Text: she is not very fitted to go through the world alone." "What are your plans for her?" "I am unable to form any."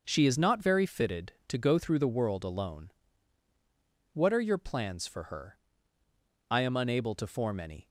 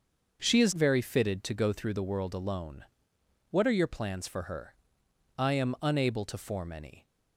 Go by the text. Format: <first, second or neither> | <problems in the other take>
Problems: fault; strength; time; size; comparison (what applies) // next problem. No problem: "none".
first | starts louder than the rest; until 1.4 s; 6.5 dB; noticeable in the first // skips "not"; at 0.7 s